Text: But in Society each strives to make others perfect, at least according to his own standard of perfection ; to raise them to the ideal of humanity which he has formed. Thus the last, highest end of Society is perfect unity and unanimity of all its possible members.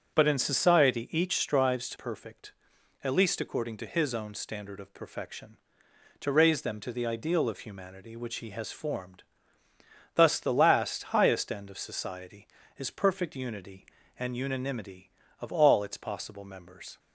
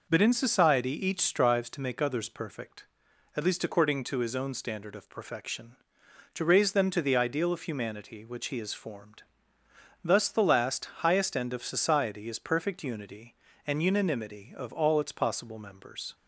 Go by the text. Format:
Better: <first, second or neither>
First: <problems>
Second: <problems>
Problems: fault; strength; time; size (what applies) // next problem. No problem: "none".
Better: second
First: starts louder than the rest; until 1.1 s; 6 dB // skips "make others"; at 1.9 s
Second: none